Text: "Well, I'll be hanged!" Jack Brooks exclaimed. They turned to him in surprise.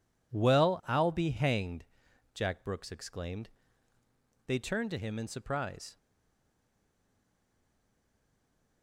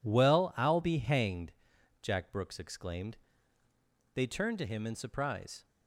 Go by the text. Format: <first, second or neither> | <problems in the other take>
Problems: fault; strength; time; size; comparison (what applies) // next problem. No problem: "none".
second | stays silent after the last word; strong; from 5.9 s on; 2.9 s long